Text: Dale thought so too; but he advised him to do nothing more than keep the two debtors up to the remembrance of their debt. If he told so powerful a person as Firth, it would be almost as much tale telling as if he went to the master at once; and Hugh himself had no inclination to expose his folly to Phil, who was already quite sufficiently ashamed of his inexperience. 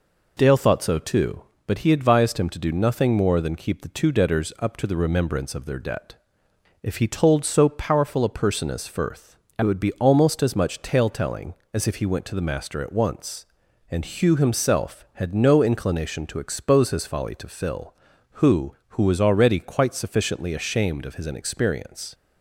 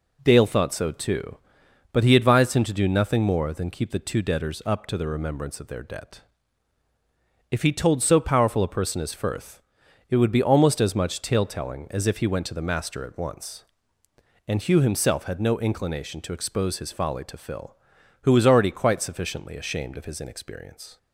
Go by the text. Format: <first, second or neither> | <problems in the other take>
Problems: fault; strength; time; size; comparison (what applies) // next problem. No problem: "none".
second | says "who" twice; at 18.8 s